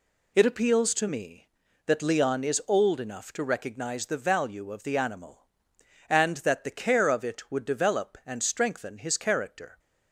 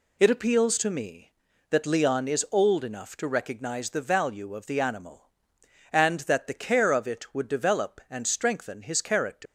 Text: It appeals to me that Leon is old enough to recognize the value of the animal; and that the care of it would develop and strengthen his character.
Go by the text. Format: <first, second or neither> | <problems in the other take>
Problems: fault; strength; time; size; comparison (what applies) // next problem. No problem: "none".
first | leaves "character" unfinished; at 9.4 s; 170 ms